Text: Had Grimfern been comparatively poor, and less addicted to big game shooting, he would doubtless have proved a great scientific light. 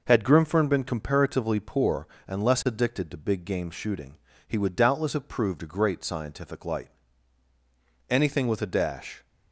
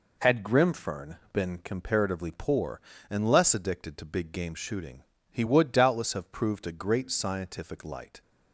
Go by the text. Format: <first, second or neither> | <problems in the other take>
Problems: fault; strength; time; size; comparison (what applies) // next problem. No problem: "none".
second | goes on to say "Anything with a dash"; noticeable; from 8.0 s on; 1.1 s long